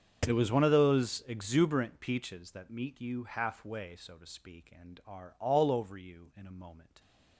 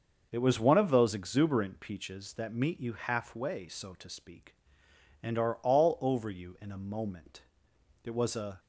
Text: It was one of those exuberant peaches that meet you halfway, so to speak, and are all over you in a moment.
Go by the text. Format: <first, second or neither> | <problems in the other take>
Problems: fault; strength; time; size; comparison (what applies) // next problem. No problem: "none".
first | starts louder than the rest; noticeable; until 1.3 s; 6 dB; strong in the first // goes on to say "It was a"; from 8.0 s on; 0.56 s long